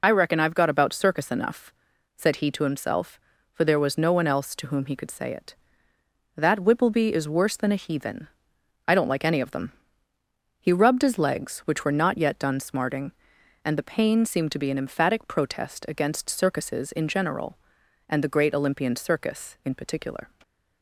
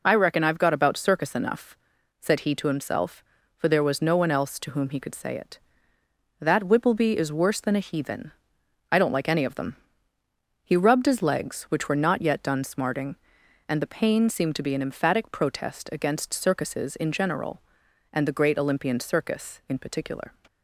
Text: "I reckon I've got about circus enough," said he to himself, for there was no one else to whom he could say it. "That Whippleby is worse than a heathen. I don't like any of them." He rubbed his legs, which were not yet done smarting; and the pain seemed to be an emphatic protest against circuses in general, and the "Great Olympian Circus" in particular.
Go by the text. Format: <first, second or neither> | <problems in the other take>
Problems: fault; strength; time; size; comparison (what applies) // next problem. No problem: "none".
second | loses the start of "I"; at 0.0 s; 35 ms